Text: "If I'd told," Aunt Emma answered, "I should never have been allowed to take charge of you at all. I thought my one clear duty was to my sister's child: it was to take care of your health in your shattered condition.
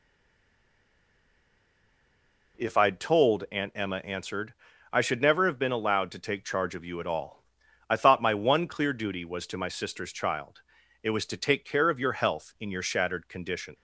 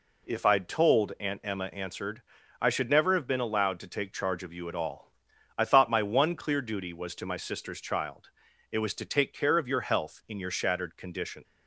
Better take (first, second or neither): second